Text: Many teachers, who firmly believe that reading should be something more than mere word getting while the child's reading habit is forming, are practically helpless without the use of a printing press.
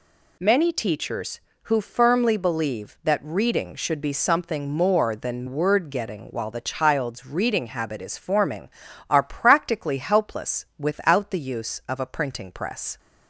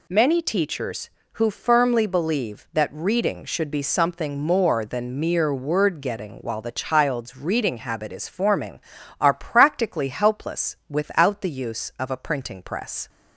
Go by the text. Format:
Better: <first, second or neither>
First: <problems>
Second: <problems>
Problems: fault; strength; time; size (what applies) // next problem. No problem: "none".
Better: second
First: skips "mere"; at 5.4 s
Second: none